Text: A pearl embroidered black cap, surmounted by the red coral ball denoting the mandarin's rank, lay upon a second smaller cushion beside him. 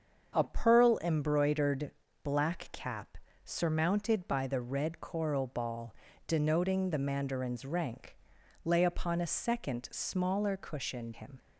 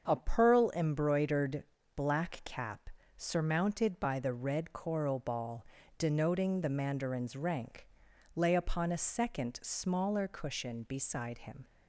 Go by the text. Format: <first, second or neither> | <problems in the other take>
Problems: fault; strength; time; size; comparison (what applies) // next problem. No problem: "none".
second | starts louder than the rest; until 1.4 s; 7 dB; also in the second // pauses between "embroidered" and "black"; slight; at 1.9 s; 0.32 s long; slight in the second // pauses between "ball" and "denoting"; slight; at 5.9 s; 0.32 s long; slight in the second // skips "beside"; at 11.1 s